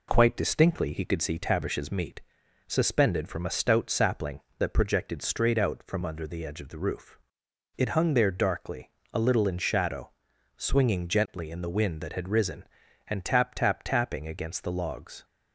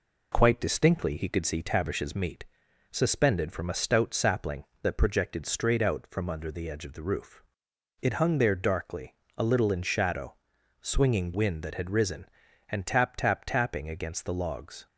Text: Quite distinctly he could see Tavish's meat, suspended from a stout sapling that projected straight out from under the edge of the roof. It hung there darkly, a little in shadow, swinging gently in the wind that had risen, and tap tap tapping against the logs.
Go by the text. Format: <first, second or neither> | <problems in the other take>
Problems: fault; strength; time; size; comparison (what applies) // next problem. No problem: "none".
first | skips "gently in the"; at 11.3 s